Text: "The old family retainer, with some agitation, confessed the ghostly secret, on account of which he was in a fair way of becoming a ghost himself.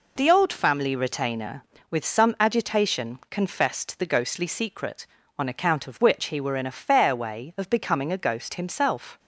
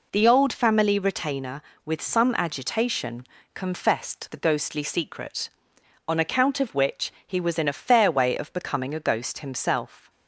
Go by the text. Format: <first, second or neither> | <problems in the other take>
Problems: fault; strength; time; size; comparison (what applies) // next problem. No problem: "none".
second | says "were" for "was"; at 6.4 s